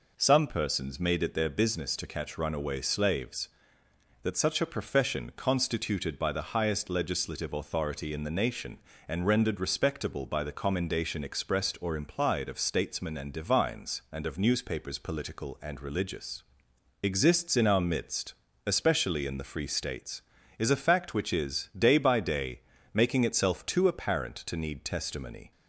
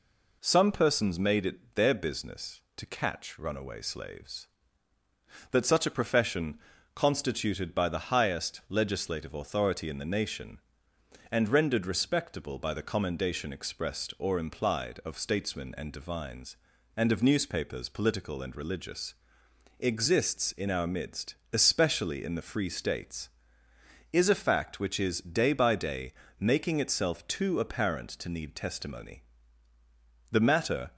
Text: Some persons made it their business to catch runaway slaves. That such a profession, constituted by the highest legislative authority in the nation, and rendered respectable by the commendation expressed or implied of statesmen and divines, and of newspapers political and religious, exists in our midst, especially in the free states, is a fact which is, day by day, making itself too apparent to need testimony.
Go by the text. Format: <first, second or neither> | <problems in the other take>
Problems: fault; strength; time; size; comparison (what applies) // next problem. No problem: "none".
first | goes on to say "The matter"; from 30.3 s on; 0.60 s long